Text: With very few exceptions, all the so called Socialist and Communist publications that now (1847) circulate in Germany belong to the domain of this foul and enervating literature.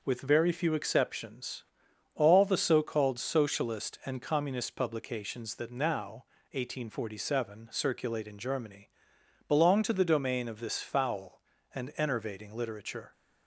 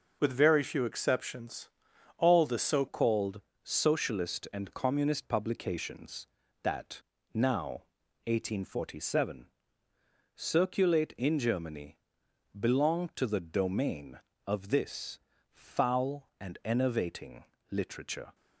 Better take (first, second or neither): first